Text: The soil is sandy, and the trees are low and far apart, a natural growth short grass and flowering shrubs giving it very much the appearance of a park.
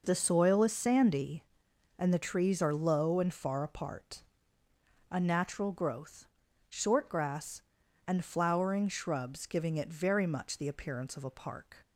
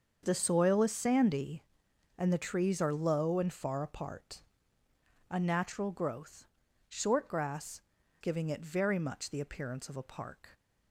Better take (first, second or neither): first